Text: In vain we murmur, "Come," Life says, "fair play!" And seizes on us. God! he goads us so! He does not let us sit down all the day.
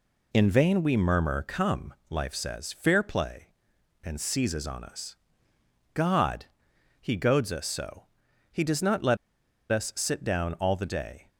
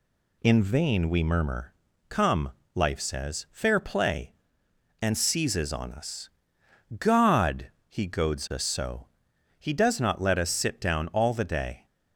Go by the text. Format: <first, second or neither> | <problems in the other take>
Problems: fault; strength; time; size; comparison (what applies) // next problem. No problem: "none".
second | pauses between "let" and "us"; noticeable; at 9.1 s; 0.54 s long